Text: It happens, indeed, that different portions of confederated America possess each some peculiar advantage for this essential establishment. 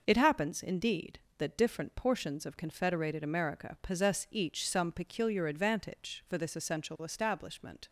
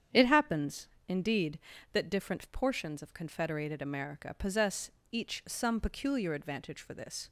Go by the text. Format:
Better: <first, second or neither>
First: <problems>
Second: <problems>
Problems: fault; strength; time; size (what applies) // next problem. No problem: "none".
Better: first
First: none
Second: starts louder than the rest; strong; until 1.3 s; 8.5 dB // pauses between "possess" and "each"; slight; at 4.8 s; 0.22 s long // stops before "essential establishment"; at 7.2 s